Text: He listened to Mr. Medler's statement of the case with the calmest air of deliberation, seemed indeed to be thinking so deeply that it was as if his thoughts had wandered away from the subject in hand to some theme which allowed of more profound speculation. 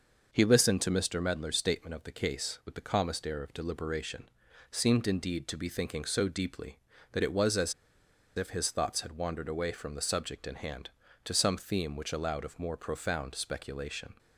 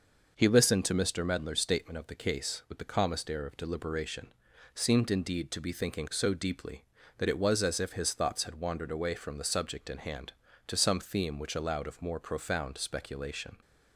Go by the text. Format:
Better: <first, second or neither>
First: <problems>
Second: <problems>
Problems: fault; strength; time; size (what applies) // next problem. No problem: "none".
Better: second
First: pauses between "as" and "if"; noticeable; at 7.7 s; 0.64 s long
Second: none